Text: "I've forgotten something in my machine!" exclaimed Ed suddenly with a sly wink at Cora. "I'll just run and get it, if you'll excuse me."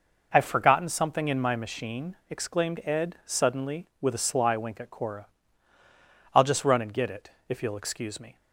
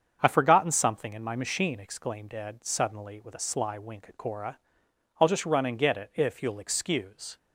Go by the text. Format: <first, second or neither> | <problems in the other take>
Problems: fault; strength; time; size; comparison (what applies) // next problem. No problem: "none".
first | starts louder than the rest; strong; until 1.2 s; 7.5 dB // stops before "me"; at 7.3 s